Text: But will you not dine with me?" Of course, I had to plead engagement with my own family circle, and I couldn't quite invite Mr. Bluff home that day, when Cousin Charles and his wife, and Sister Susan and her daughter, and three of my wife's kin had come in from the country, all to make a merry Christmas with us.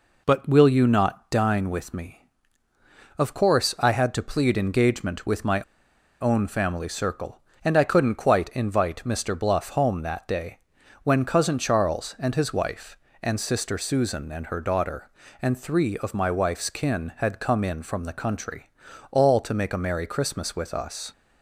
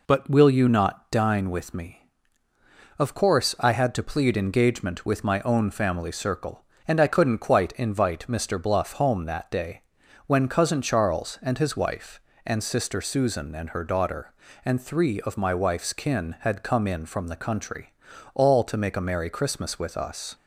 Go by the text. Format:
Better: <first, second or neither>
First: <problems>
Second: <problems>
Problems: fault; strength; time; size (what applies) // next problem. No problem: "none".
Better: second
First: pauses between "my" and "own"; noticeable; at 5.5 s; 0.60 s long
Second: none